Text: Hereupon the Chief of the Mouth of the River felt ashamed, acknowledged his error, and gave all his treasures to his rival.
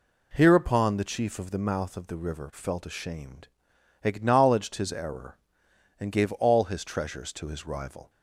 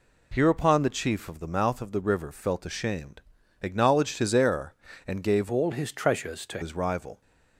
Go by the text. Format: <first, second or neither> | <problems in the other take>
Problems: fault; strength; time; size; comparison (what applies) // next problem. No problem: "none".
first | changes voice from "all" to "to"; from 5.5 to 6.6 s; 1.1 s long